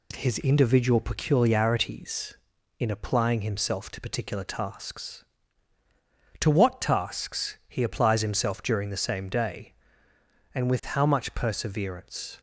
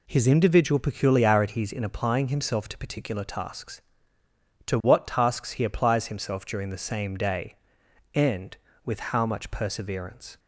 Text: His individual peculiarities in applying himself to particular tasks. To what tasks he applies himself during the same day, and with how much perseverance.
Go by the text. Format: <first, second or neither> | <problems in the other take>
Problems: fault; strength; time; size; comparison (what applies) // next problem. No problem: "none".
neither | none